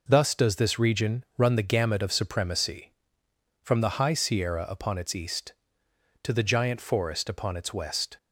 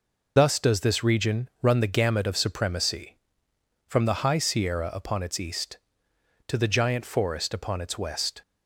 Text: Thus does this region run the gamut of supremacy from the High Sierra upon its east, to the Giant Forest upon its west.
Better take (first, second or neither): first